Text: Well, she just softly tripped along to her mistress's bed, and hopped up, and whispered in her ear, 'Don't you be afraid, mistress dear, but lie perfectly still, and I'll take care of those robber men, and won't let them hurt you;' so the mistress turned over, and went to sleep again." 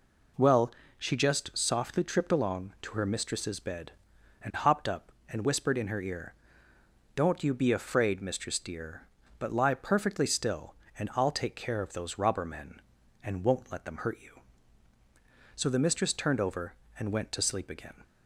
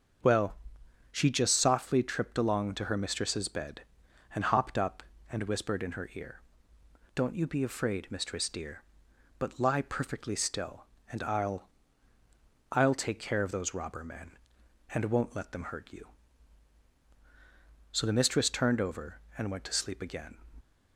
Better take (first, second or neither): first